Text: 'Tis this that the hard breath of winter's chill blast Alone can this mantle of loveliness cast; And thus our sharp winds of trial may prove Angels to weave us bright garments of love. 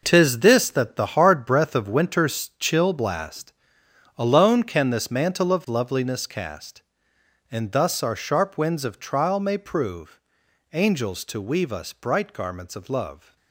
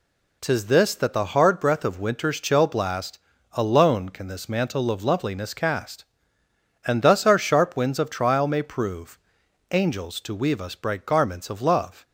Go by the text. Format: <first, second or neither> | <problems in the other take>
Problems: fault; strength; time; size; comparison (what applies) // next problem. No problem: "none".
second | gets quieter; strong; throughout; 11 dB // pauses between "blast" and "Alone"; noticeable; at 3.5 s; 0.64 s long; also in the second // pauses between "prove" and "Angels"; noticeable; at 10.1 s; 0.52 s long; noticeable in the second